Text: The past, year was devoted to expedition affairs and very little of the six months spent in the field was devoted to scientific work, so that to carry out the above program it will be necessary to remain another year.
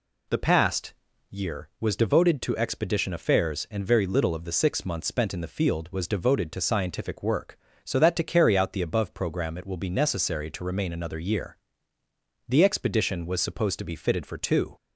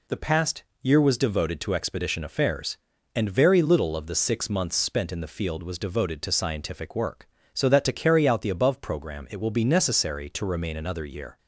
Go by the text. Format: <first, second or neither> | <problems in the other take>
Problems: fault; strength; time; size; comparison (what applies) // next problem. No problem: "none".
second | goes on to say "The expedition was supposed to be fitted for two"; strong; from 12.4 s on; 2.2 s long